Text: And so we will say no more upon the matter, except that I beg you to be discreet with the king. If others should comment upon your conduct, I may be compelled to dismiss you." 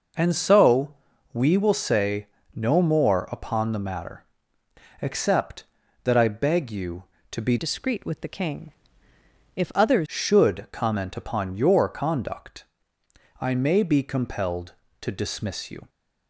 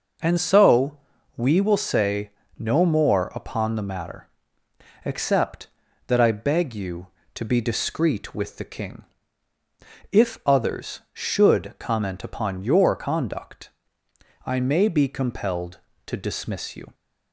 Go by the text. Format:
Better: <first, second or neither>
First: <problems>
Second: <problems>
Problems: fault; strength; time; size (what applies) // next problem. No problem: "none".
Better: second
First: pauses between "so" and "we"; at 0.9 s; 0.38 s long // pauses between "say" and "no"; slight; at 2.2 s; 0.28 s long // changes voice from "discreet" to "others"; from 7.5 to 10.0 s; 2.5 s long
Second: pauses between "so" and "we"; at 0.9 s; 0.38 s long // pauses between "say" and "no"; slight; at 2.2 s; 0.28 s long